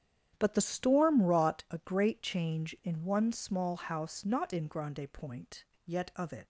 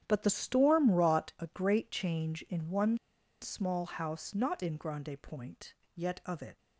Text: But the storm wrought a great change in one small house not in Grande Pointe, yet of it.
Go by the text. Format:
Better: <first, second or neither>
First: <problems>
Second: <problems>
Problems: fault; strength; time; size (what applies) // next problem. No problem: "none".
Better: first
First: starts louder than the rest; strong; until 1.3 s; 9.5 dB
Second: starts louder than the rest; strong; until 1.0 s; 9.5 dB // pauses between "one" and "small"; at 2.9 s; 0.44 s long